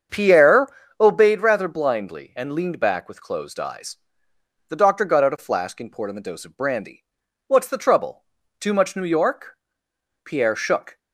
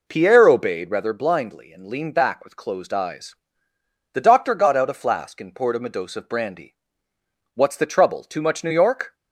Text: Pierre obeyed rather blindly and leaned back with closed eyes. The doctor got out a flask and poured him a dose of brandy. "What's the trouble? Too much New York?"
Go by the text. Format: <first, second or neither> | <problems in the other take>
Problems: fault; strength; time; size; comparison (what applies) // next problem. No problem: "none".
second | starts louder than the rest; strong; until 1.4 s; 7 dB // pauses between "Pierre" and "obeyed"; slight; at 0.6 s; 0.32 s long // goes on to say "Pierre shook"; noticeable; from 10.2 s on; 0.74 s long